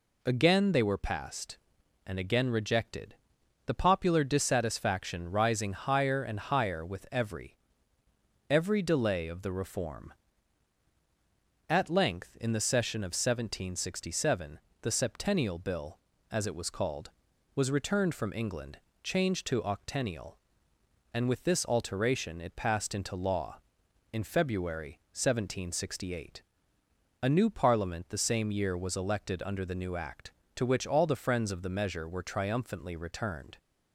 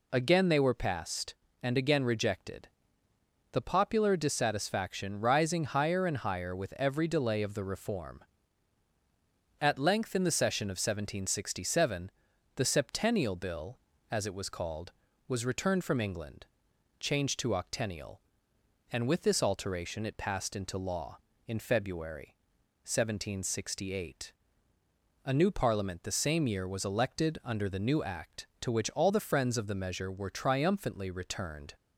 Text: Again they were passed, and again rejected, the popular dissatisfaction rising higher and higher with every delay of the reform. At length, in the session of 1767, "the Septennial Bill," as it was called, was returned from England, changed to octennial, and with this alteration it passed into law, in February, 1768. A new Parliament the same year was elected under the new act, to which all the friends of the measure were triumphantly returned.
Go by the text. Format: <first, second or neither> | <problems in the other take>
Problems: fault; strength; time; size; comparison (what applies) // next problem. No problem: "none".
second | says "every" twice; at 8.4 s